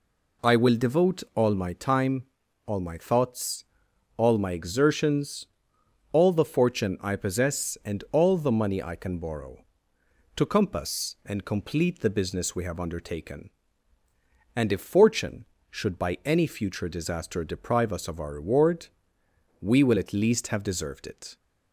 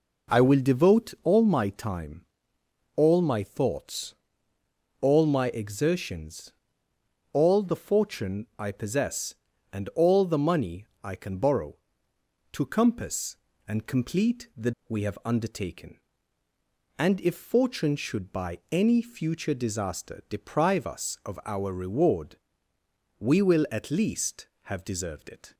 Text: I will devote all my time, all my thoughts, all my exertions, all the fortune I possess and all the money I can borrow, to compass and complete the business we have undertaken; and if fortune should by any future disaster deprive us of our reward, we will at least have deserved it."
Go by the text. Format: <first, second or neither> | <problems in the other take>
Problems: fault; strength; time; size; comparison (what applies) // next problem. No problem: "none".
first | pauses between "money" and "I"; slight; at 10.8 s; 0.18 s long // skips "business"; at 14.7 s